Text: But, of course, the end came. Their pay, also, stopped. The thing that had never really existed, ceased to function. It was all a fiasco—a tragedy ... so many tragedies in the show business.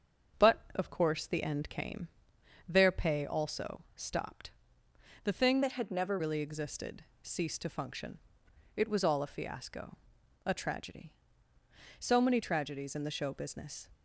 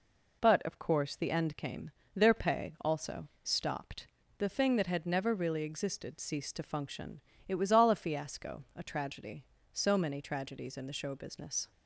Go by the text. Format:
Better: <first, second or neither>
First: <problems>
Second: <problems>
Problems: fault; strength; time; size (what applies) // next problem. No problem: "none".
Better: second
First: starts louder than the rest; strong; until 1.5 s; 7.5 dB // changes voice from "that" to "never"; from 5.6 to 6.1 s; 0.5 s long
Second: none